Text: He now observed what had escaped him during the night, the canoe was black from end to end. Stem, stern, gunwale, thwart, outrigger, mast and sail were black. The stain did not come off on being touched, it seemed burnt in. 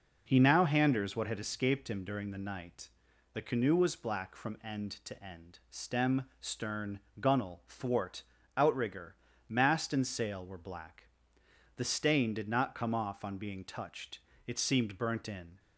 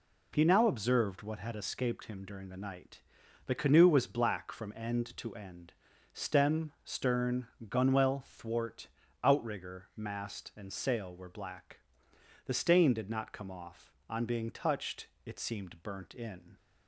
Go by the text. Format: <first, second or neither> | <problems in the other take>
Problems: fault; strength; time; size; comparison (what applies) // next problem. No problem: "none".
second | says "handers" for "observed"; at 0.6 s